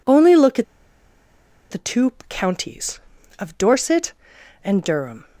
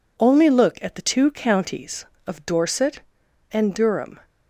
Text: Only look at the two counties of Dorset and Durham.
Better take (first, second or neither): second